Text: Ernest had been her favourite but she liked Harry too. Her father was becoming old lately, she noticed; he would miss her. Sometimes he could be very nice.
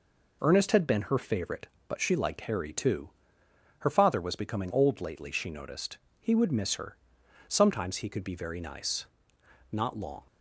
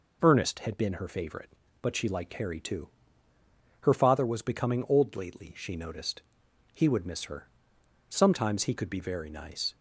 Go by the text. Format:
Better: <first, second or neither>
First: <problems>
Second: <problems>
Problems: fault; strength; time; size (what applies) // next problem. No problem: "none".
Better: second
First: goes on to say "Not long"; from 9.7 s on; 0.56 s long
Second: none